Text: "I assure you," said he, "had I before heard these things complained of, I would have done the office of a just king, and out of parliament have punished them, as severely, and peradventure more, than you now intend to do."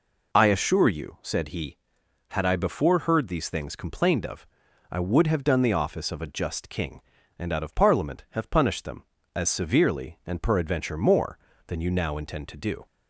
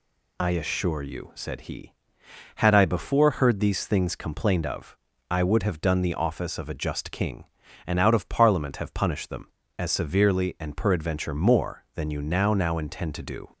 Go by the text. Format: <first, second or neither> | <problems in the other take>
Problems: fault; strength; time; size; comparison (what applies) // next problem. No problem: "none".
first | says "now" twice; at 12.5 s